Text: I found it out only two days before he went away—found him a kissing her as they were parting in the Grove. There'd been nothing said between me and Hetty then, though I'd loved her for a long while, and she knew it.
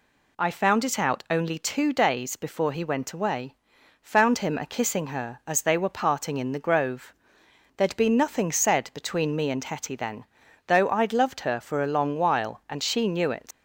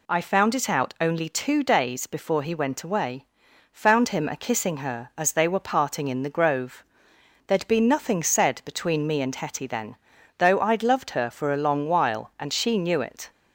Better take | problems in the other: second | leaves "it" unfinished; at 13.5 s; 90 ms

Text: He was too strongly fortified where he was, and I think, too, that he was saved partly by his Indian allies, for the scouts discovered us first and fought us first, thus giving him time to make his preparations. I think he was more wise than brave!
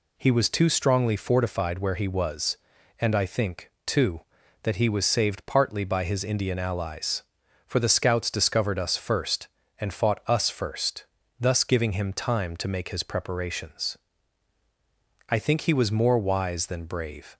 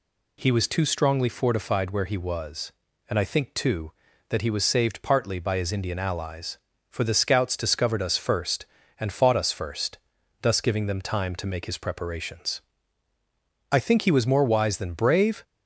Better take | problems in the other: first | says "them" for "him"; at 10.8 s

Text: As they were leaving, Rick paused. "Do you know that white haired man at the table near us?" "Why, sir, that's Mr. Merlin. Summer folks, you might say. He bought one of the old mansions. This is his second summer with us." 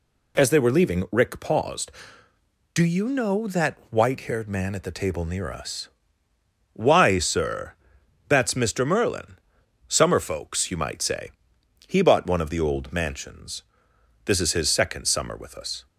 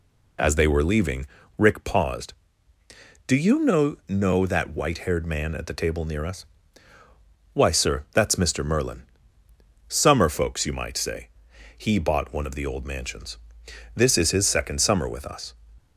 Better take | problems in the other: first | says "know" twice; at 4.0 s

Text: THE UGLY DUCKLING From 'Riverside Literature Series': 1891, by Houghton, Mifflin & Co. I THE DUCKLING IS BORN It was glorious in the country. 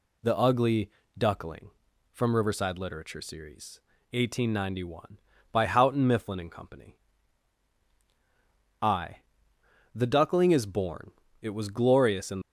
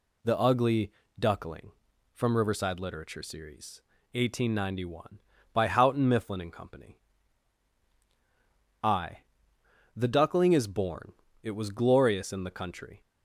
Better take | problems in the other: second | pauses between "UGLY" and "DUCKLING"; slight; at 0.8 s; 0.28 s long; slight in the second // pauses between "I" and "THE"; noticeable; at 9.1 s; 0.76 s long; noticeable in the second // pauses between "BORN" and "It"; slight; at 11.1 s; 0.30 s long; slight in the second // stops before "the country"; at 12.4 s

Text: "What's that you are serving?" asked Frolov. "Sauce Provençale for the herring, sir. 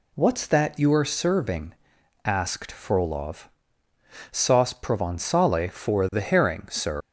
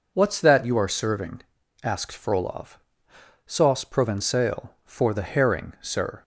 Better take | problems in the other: second | leaves "sir" unfinished; at 7.0 s; 115 ms

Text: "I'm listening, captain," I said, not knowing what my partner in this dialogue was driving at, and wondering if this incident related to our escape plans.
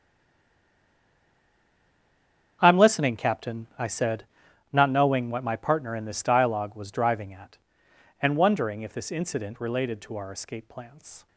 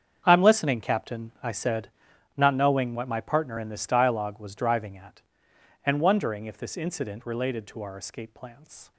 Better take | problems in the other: second | stays silent before the first word; strong; until 2.6 s; 2.6 s long // starts louder than the rest; strong; until 3.6 s; 7.5 dB; strong in the second

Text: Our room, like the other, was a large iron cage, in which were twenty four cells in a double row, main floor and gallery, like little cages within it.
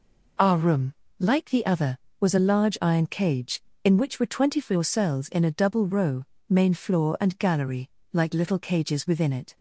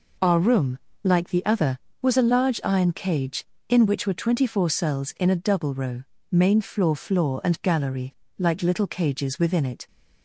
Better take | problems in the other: first | says "floor" twice; at 6.9 s

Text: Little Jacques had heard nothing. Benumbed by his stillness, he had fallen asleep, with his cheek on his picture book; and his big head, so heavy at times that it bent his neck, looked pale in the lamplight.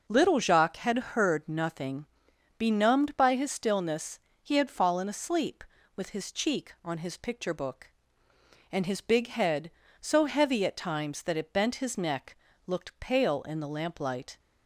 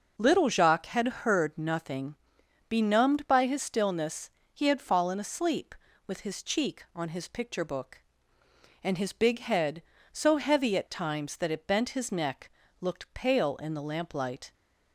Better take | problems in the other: neither | starts louder than the rest; noticeable; the same in both

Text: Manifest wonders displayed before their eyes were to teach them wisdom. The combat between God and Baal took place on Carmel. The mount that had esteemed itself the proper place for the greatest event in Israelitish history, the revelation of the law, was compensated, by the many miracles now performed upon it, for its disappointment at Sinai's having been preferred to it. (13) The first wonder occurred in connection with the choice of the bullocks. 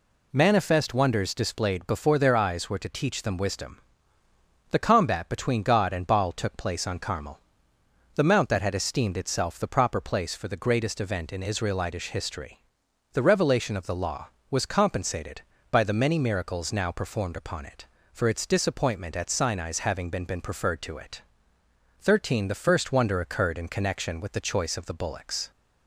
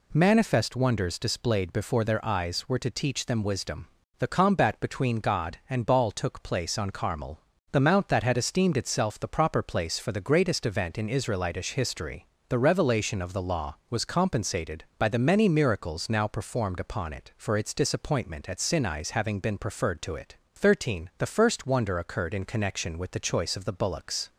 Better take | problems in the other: second | says "been" twice; at 20.2 s

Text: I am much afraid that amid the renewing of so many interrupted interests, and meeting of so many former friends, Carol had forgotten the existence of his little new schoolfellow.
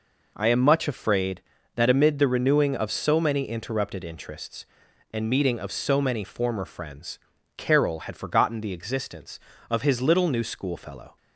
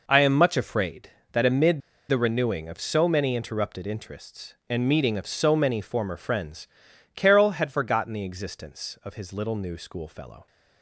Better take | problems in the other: first | pauses between "amid" and "the"; slight; at 1.7 s; 0.29 s long

